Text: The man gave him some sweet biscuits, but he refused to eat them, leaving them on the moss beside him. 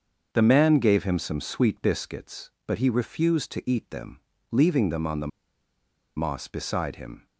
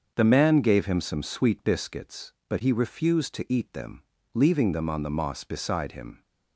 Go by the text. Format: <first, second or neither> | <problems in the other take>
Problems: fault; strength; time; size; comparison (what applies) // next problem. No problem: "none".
second | starts louder than the rest; until 1.3 s; 6.5 dB; also in the second // pauses between "the" and "moss"; noticeable; at 5.2 s; 0.89 s long